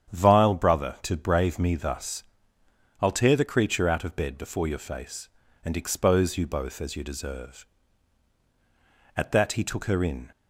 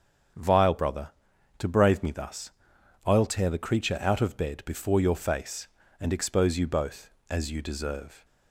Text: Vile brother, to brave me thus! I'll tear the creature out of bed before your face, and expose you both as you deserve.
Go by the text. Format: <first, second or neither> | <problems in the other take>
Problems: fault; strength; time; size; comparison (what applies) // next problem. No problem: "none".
second | starts louder than the rest; strong; until 1.1 s; 9 dB; strong in the second // goes on to say "At that he took her in"; noticeable; from 9.1 s on; 1.1 s long